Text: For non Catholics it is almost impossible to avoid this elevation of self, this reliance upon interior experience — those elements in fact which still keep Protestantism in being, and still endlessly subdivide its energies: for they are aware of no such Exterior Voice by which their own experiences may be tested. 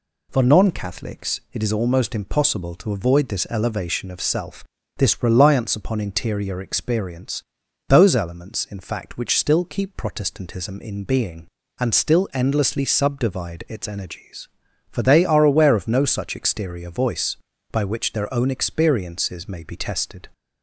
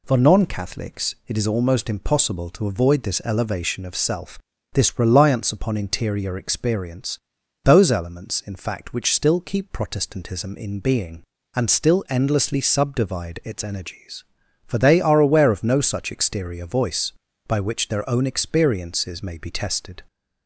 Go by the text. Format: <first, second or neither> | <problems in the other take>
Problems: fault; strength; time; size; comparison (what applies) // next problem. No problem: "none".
neither | none